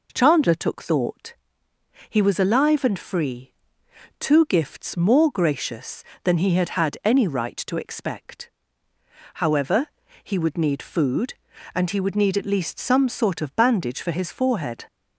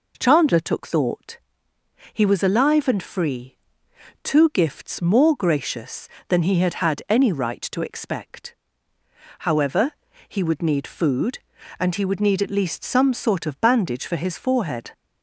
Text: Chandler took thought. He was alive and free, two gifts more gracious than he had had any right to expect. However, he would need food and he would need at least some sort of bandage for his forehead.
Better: neither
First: none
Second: none

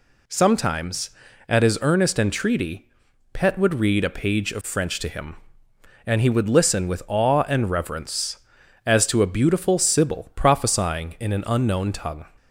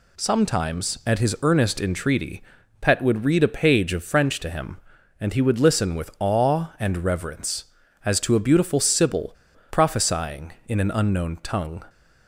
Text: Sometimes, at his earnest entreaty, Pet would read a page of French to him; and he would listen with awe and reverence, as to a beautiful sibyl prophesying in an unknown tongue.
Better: first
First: none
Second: pauses between "sibyl" and "prophesying"; slight; at 9.3 s; 0.35 s long

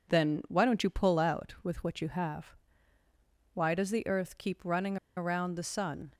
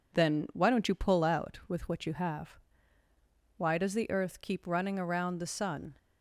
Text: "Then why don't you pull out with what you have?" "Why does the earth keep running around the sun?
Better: second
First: pauses between "running" and "around"; slight; at 4.9 s; 0.19 s long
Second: none

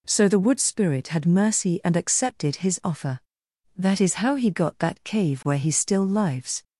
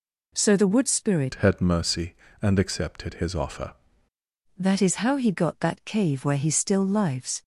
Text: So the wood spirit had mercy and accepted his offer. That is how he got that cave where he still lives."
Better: first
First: none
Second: changes voice from "had" to "offer"; from 1.3 to 3.7 s; 2.4 s long

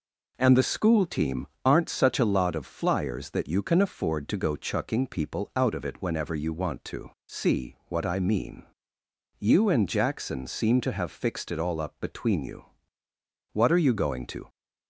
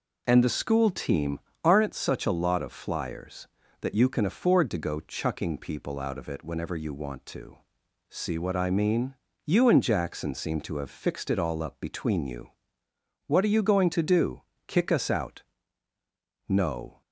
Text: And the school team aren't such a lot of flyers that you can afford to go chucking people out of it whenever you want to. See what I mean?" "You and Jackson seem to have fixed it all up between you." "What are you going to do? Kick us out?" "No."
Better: second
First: pauses between "team" and "aren't"; slight; at 1.4 s; 0.18 s long // stops before "do Kick us out No"; at 14.4 s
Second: pauses between "team" and "aren't"; slight; at 1.3 s; 0.24 s long

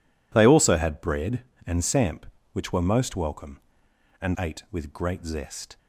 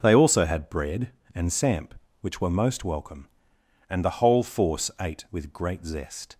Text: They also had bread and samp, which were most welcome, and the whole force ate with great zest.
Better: second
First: skips "the whole force"; at 4.3 s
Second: none

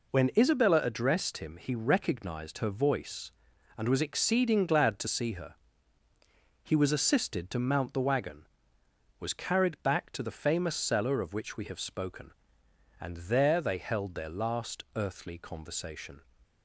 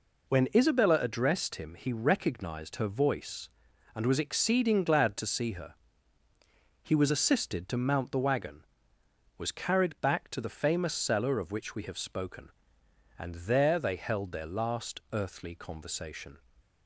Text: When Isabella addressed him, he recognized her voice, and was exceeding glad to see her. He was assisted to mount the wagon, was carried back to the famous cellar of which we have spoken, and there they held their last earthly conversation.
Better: neither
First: none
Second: none

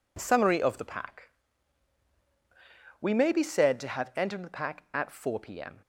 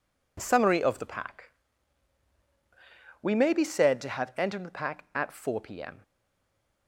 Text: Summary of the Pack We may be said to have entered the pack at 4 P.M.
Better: first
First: pauses between "Pack" and "We"; strong; at 1.2 s; 1.7 s long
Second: pauses between "Pack" and "We"; strong; at 1.5 s; 1.7 s long // stays silent after the last word; slight; from 6.0 s on; 0.8 s long

